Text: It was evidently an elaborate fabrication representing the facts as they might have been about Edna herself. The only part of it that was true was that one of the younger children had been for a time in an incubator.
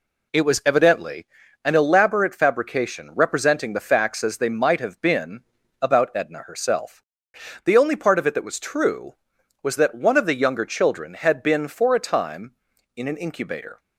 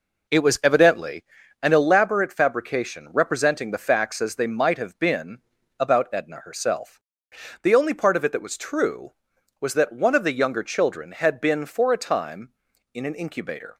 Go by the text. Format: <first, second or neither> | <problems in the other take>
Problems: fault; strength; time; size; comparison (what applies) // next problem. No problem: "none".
first | starts louder than the rest; noticeable; until 2.0 s; 4.5 dB // pauses between "evidently" and "an"; at 1.2 s; 0.40 s long; also in the first // pauses between "been" and "about"; at 5.3 s; 0.40 s long; also in the first